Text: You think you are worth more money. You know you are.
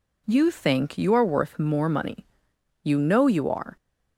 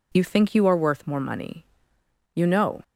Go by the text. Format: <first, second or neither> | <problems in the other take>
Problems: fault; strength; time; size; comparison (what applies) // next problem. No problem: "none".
first | stops before "you are"; at 2.8 s